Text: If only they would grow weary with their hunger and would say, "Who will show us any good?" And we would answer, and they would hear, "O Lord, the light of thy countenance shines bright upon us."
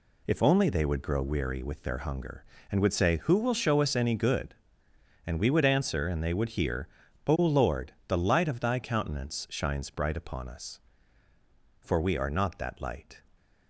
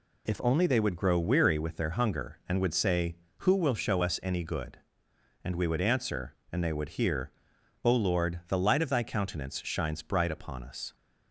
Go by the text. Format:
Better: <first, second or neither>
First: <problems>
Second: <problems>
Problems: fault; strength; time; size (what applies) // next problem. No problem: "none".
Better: second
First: goes on to say "For we are not that Light"; from 11.8 s on; 1.3 s long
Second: none